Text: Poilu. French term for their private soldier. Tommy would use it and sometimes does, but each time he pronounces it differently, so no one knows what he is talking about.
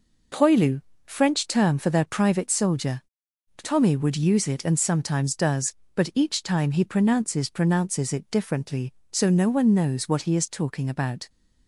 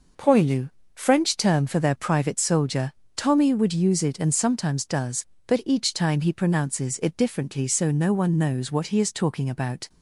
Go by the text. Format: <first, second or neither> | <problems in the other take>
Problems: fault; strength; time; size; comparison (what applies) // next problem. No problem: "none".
second | says "pronounces" twice; at 7.5 s